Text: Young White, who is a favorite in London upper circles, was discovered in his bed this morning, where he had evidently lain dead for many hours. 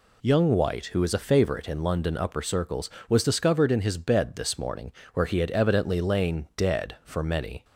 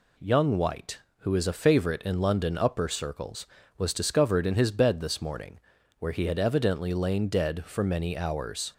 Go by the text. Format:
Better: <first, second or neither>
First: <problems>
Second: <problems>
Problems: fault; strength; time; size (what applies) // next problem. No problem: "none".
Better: second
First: stops before "hours"; at 7.6 s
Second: none